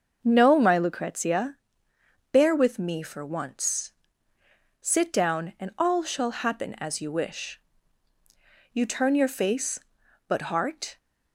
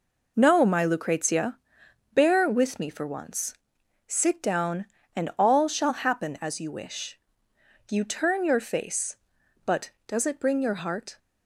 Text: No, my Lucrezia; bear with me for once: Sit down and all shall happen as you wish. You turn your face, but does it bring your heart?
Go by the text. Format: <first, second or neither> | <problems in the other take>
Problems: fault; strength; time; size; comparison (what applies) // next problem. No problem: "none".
second | starts louder than the rest; until 1.2 s; 6 dB // skips "does it bring your"; at 10.5 s